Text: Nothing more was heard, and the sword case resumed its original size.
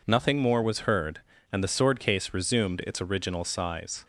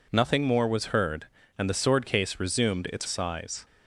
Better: first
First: none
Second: skips "original"; at 3.0 s

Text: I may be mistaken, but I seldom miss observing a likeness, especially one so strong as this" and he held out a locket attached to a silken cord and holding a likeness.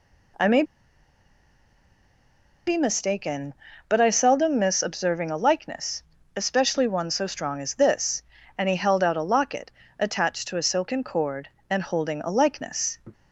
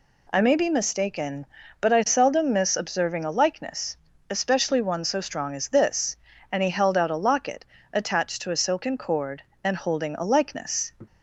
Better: second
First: pauses between "may" and "be"; strong; at 0.6 s; 2.0 s long // pauses between "locket" and "attached"; slight; at 9.6 s; 0.28 s long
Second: pauses between "locket" and "attached"; slight; at 7.6 s; 0.28 s long

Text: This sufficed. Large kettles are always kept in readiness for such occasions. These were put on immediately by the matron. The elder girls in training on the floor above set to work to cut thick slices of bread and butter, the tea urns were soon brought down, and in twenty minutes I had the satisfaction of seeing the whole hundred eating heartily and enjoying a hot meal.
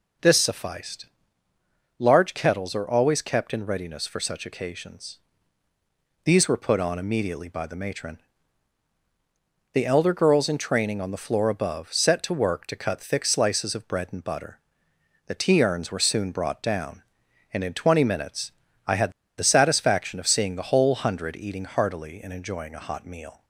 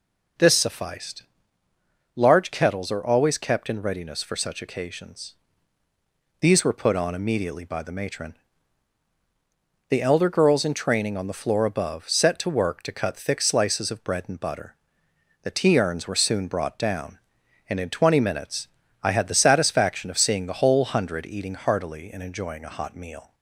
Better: second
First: pauses between "minutes" and "I"; slight; at 18.5 s; 0.36 s long // pauses between "had" and "the"; slight; at 19.1 s; 0.26 s long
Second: pauses between "minutes" and "I"; slight; at 18.6 s; 0.36 s long

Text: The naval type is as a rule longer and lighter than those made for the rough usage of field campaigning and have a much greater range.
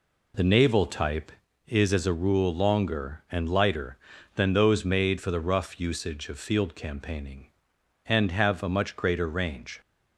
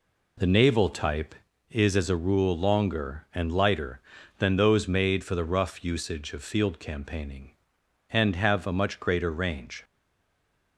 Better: first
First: none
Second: stays silent after the last word; slight; from 9.8 s on; 0.9 s long

